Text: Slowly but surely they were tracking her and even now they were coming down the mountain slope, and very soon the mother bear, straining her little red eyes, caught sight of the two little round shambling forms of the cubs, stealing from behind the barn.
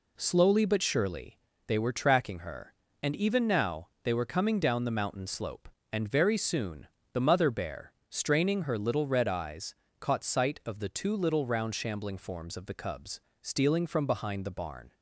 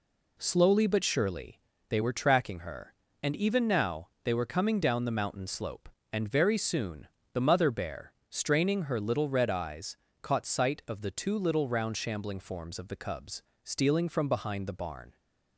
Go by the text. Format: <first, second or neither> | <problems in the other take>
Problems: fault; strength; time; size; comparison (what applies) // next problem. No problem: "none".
neither | pauses between "surely" and "they"; slight; the same in both // pauses between "now" and "they"; slight; the same in both // pauses between "soon" and "the"; slight; the same in both